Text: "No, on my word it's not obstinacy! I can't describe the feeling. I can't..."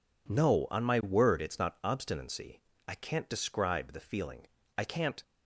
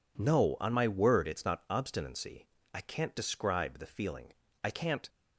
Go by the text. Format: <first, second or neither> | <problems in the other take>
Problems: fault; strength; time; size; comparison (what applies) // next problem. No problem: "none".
neither | none